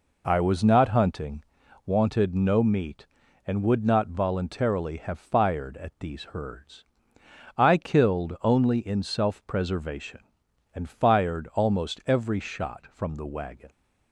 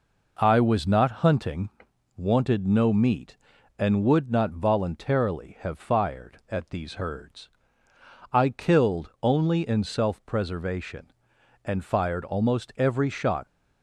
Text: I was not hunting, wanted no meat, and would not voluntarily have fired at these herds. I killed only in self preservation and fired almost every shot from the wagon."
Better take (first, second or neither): first